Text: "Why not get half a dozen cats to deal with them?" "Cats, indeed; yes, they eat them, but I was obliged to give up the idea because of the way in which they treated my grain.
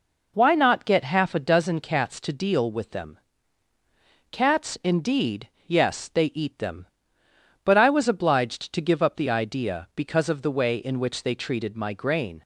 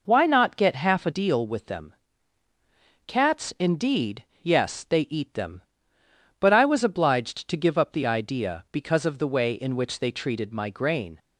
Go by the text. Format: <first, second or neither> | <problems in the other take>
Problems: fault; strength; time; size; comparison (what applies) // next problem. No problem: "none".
first | skips "dozen cats to"; at 1.1 s